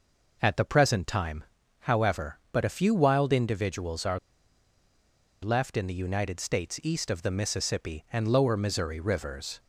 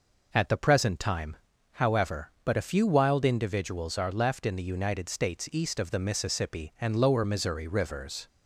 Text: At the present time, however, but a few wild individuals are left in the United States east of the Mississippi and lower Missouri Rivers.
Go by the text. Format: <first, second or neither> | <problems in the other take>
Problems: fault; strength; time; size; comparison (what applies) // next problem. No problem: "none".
second | pauses between "are" and "left"; at 4.1 s; 1.2 s long